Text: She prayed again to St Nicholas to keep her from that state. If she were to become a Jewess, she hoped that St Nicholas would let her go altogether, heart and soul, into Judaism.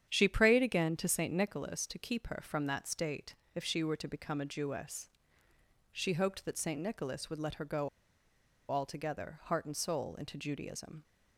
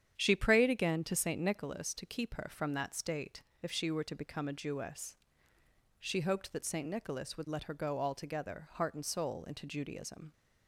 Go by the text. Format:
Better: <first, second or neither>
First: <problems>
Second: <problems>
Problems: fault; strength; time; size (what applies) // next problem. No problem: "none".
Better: second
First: starts louder than the rest; strong; until 1.0 s; 9 dB // pauses between "go" and "altogether"; noticeable; at 7.8 s; 0.80 s long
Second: starts louder than the rest; strong; until 1.1 s; 9 dB